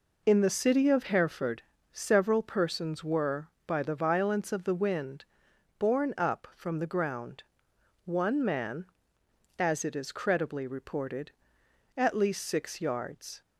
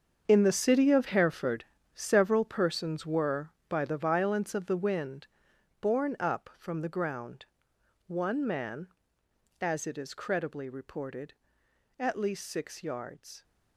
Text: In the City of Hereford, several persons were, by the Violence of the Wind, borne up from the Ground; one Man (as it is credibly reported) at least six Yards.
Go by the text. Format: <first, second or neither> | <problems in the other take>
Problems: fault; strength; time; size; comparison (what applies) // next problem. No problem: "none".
first | gets quieter; strong; throughout; 12.5 dB